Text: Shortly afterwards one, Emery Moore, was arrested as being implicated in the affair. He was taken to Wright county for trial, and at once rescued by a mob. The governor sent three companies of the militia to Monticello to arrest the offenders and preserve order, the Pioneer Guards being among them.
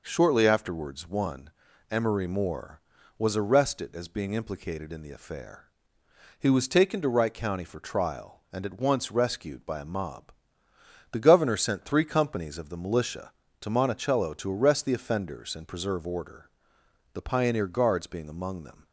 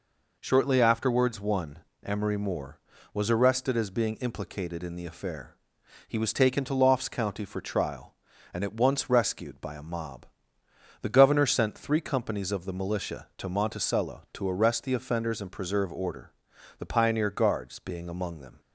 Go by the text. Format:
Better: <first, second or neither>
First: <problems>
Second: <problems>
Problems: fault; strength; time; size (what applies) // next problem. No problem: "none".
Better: first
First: none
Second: says "Lofts" for "Wright"; at 6.7 s